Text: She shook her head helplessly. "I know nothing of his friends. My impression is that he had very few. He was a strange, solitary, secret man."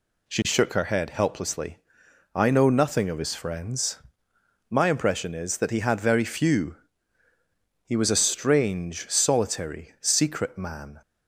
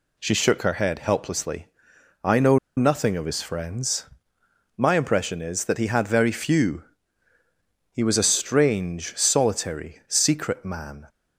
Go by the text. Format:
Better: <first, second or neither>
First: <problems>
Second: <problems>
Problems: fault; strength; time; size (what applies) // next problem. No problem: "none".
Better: first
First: none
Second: pauses between "know" and "nothing"; slight; at 2.5 s; 0.18 s long